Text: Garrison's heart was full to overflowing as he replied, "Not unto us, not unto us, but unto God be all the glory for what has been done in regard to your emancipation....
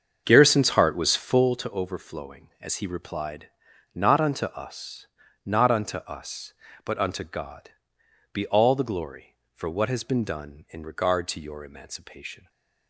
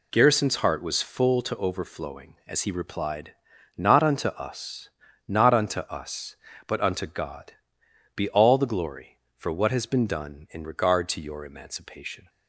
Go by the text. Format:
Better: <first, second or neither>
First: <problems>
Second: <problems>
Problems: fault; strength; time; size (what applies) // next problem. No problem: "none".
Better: second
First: starts louder than the rest; until 1.6 s; 7 dB // pauses between "God" and "be"; noticeable; at 7.6 s; 0.62 s long // stays silent after the last word; slight; from 12.3 s on; 0.5 s long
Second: pauses between "God" and "be"; noticeable; at 7.5 s; 0.62 s long